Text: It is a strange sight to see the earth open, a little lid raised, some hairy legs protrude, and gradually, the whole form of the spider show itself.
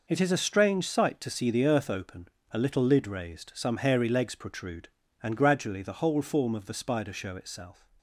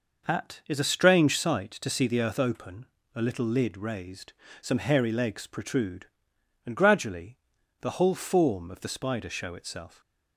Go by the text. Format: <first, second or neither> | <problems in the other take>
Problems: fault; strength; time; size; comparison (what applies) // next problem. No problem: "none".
first | says "At" for "It"; at 0.2 s